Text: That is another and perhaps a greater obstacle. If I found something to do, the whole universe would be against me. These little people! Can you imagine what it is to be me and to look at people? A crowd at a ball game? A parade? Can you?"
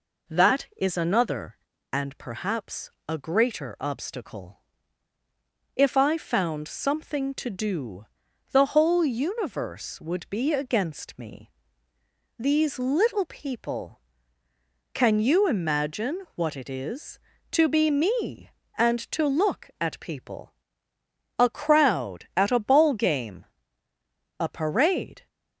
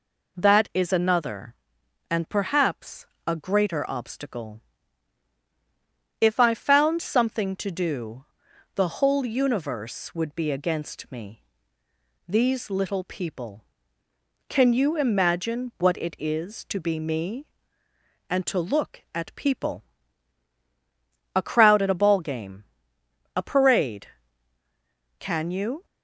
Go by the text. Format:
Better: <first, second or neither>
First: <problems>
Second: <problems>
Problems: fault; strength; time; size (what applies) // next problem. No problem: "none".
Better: second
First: pauses between "perhaps" and "a"; slight; at 2.9 s; 0.16 s long // stops before "Can you"; at 25.2 s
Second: pauses between "perhaps" and "a"; slight; at 3.0 s; 0.20 s long